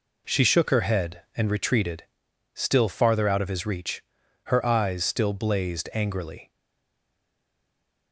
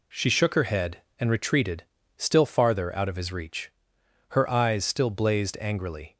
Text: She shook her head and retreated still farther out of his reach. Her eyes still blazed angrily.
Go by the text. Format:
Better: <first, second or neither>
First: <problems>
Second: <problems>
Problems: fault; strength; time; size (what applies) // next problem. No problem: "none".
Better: second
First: pauses between "retreated" and "still"; noticeable; at 2.0 s; 0.52 s long // stays silent after the last word; noticeable; from 6.5 s on; 1.6 s long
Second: pauses between "retreated" and "still"; slight; at 1.8 s; 0.34 s long